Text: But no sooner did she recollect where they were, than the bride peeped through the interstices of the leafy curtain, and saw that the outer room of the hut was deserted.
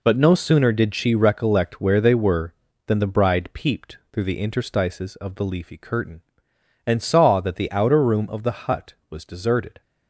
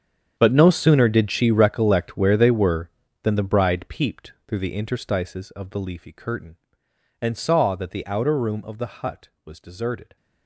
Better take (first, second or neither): first